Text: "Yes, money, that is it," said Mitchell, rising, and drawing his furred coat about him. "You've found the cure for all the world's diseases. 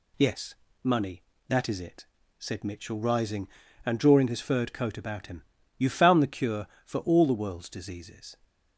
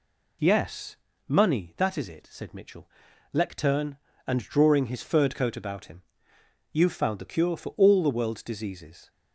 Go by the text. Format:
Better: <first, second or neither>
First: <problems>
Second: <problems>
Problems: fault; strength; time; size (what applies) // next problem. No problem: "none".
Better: first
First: none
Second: says "lectern" for "rising"; at 3.3 s